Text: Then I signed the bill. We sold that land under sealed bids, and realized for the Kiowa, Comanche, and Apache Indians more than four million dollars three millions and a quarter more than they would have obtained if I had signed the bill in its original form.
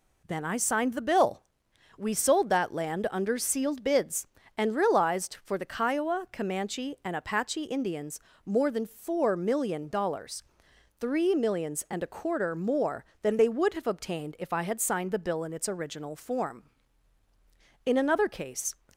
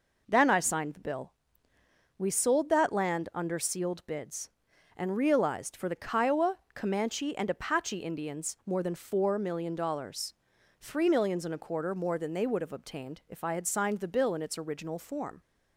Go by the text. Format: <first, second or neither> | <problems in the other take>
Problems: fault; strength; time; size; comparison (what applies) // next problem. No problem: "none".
second | pauses between "Indians" and "more"; slight; at 8.1 s; 0.26 s long // pauses between "dollars" and "three"; noticeable; at 10.4 s; 0.58 s long; noticeable in the second // goes on to say "In another case"; noticeable; from 17.8 s on; 0.92 s long